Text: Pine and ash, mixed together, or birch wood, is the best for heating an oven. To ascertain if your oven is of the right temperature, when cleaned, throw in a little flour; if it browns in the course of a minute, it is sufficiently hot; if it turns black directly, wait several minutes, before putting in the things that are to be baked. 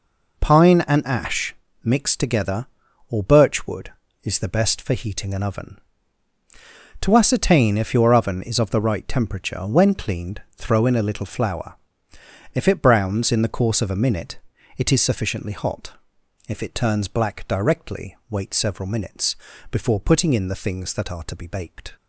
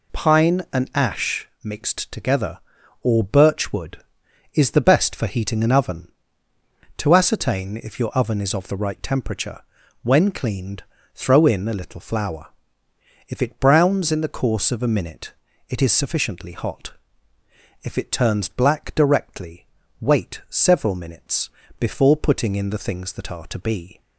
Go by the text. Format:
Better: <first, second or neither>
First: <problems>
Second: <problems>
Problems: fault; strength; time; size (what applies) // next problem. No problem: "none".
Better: first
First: none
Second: stops before "baked"; at 24.0 s